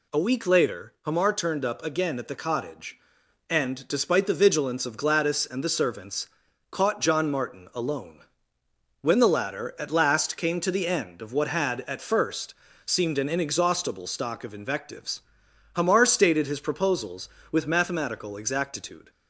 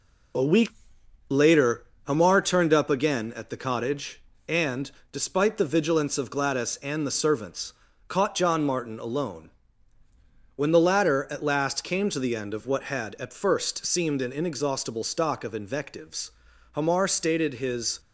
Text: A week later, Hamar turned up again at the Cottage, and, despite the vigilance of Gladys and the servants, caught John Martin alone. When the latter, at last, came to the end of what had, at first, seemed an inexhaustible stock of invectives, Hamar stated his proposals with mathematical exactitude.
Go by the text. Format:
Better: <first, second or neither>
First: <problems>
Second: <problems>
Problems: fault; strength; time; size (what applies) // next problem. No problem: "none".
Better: first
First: none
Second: pauses between "week" and "later"; noticeable; at 0.6 s; 0.62 s long // stops before "proposals with mathematical exactitude"; at 17.9 s